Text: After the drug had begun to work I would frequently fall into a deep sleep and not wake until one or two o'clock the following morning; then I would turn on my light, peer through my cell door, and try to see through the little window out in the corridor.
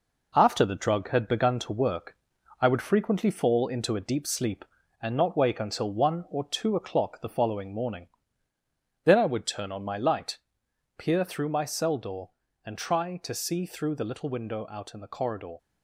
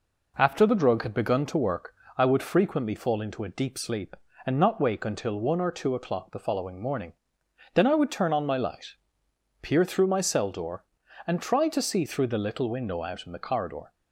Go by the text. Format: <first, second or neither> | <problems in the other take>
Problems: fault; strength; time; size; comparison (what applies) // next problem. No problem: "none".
second | gets quieter; noticeable; throughout; 4.5 dB // pauses between "work" and "I"; noticeable; at 2.1 s; 0.46 s long; slight in the second